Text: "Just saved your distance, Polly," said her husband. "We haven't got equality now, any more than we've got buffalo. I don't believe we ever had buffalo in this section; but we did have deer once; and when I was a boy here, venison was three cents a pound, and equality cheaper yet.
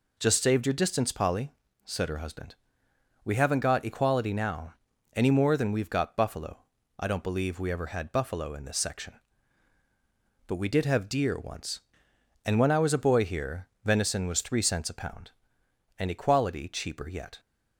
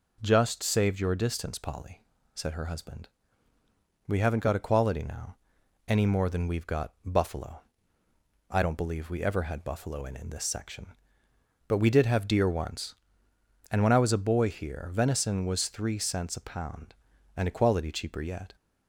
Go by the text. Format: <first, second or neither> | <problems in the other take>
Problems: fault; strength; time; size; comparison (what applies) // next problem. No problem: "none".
first | says "in" twice; at 10.1 s